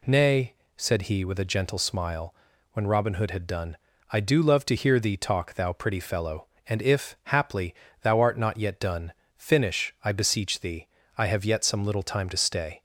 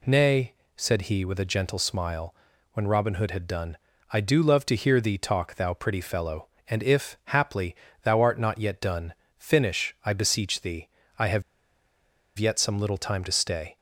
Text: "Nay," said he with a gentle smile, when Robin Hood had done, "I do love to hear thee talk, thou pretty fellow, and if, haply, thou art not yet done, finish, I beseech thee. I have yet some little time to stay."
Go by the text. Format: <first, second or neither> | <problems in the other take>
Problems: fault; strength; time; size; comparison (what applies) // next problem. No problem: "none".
first | pauses between "have" and "yet"; noticeable; at 11.4 s; 0.96 s long